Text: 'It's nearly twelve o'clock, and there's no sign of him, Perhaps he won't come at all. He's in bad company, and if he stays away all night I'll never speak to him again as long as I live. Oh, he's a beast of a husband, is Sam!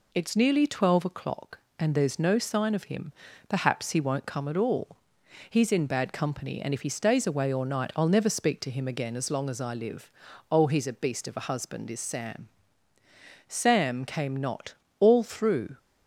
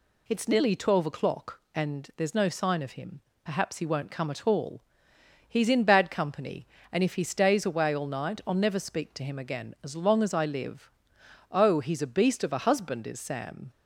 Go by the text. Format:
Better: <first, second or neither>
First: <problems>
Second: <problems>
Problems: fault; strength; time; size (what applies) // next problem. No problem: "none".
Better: second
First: goes on to say "Sam came not All through"; strong; from 13.4 s on; 2.3 s long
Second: none